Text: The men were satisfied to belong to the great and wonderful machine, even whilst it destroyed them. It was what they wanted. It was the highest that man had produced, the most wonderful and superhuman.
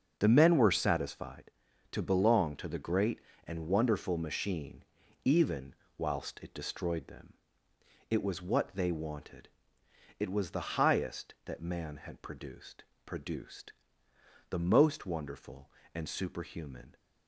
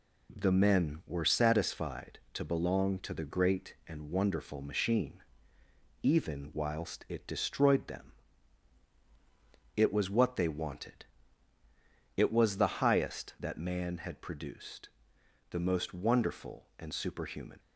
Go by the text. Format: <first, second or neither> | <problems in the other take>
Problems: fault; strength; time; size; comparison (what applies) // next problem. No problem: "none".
second | starts louder than the rest; until 1.2 s; 6 dB // pauses between "even" and "whilst"; slight; at 5.7 s; 0.22 s long // says "produced" twice; at 13.0 s